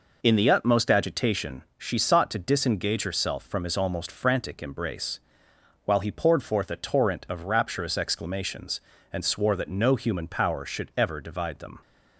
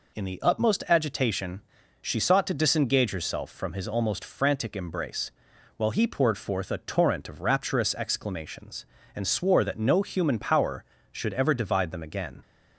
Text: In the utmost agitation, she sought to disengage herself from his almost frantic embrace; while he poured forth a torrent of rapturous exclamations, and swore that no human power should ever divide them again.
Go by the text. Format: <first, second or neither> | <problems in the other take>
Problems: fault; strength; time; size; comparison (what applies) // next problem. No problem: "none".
second | stops before "again"; at 11.8 s